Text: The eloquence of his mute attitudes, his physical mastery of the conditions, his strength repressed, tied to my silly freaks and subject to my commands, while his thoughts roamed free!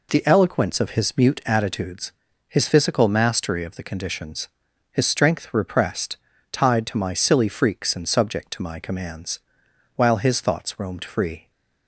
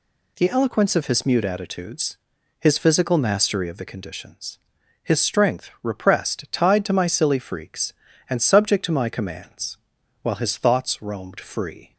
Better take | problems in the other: neither | none

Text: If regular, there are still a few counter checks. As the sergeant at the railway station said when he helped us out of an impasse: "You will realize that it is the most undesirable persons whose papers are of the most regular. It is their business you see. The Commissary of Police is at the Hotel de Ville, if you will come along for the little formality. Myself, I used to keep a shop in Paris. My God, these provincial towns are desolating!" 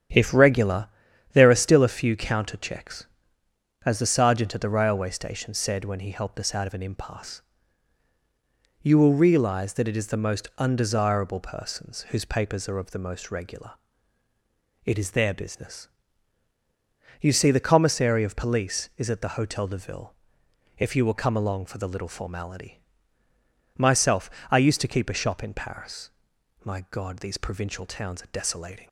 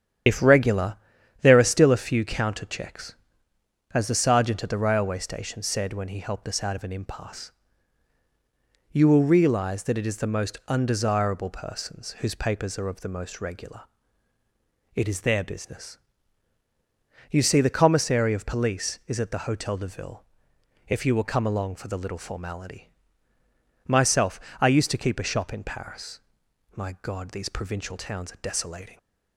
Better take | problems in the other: first | loses the start of "If"; at 0.2 s; 75 ms // starts louder than the rest; strong; until 1.6 s; 9.5 dB; strong in the first // pauses between "business" and "you"; strong; at 15.9 s; 1.3 s long; strong in the first

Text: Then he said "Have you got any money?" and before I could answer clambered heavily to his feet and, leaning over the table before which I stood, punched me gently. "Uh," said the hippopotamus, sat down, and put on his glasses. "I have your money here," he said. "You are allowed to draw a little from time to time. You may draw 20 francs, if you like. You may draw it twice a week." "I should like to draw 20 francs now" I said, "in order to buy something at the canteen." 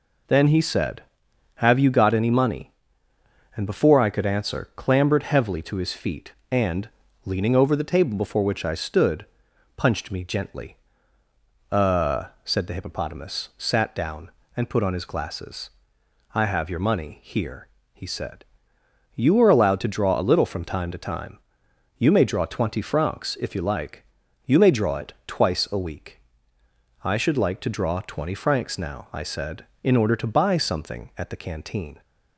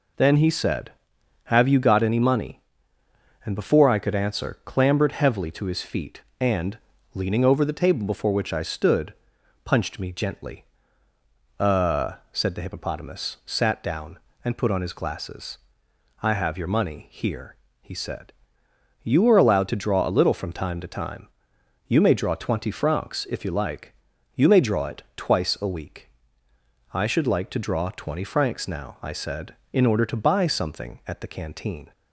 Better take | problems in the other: neither | none

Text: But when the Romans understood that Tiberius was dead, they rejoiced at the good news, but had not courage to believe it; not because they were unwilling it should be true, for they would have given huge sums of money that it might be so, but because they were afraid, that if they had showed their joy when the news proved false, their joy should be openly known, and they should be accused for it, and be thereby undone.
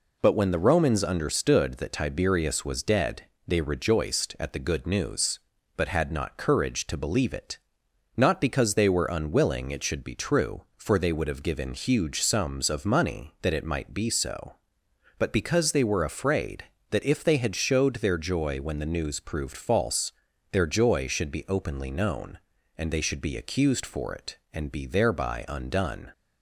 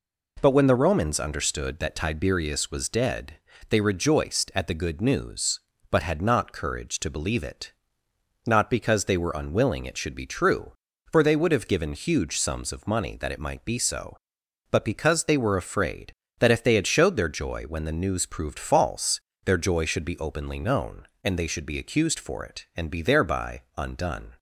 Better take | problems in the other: neither | none

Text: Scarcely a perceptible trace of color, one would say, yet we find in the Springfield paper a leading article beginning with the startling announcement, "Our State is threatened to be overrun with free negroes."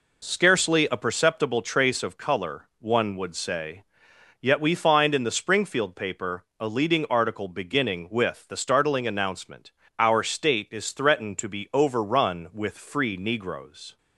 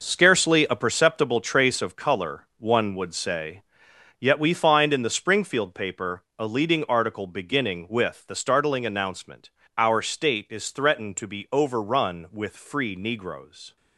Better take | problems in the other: first | gets quieter; strong; throughout; 9.5 dB // pauses between "paper" and "a"; slight; at 6.2 s; 0.16 s long; slight in the first

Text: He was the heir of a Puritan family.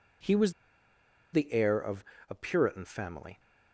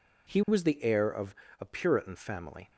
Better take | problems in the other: second | pauses between "was" and "the"; noticeable; at 0.5 s; 0.81 s long // pauses between "of" and "a"; slight; at 2.0 s; 0.26 s long; slight in the second

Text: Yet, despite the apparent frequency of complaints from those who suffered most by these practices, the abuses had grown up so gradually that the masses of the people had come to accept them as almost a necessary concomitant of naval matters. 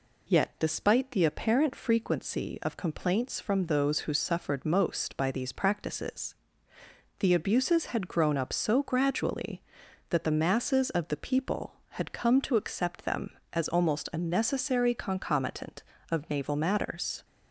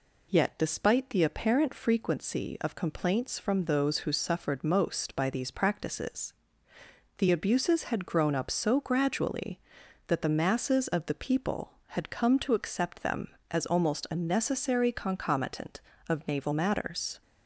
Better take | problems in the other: neither | none

